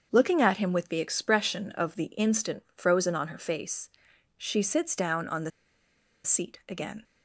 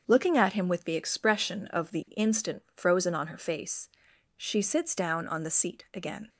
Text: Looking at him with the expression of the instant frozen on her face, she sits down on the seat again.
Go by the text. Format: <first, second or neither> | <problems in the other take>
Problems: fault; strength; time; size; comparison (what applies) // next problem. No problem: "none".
second | starts louder than the rest; until 1.1 s; 7 dB; also in the second // pauses between "the" and "seat"; noticeable; at 5.5 s; 0.74 s long